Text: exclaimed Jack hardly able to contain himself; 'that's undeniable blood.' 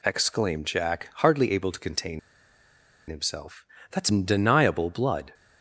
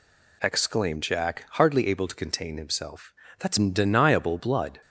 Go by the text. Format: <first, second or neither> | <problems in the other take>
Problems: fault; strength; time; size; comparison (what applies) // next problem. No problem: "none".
second | pauses between "contain" and "himself"; noticeable; at 2.1 s; 0.89 s long